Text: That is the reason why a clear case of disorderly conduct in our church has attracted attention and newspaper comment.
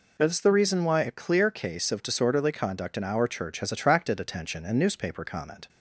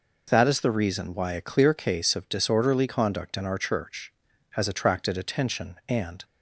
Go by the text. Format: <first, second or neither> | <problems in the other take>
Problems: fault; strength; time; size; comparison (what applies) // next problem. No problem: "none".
first | stops before "newspaper comment"; at 6.2 s